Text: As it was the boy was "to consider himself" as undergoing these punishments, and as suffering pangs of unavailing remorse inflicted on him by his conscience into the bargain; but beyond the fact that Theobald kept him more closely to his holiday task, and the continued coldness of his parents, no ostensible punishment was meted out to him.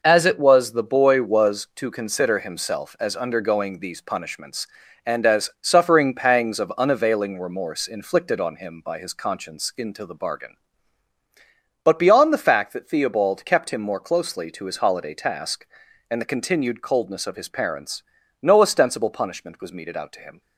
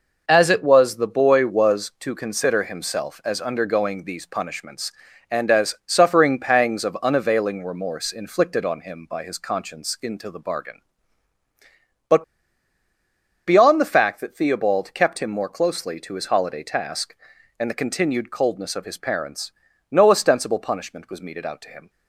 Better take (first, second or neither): first